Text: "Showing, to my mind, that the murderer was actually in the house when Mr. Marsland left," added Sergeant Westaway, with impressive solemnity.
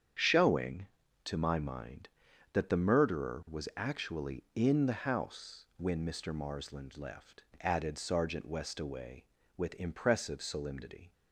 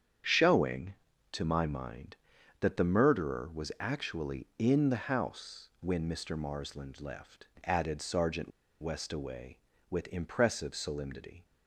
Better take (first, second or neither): first